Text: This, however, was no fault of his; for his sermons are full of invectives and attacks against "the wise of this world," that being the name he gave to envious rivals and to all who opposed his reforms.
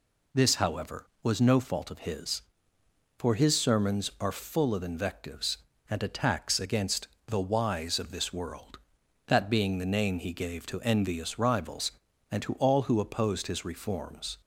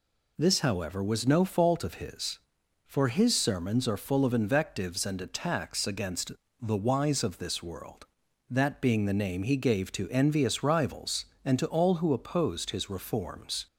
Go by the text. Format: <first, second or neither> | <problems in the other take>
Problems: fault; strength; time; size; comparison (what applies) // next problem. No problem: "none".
neither | pauses between "against" and "the"; slight; the same in both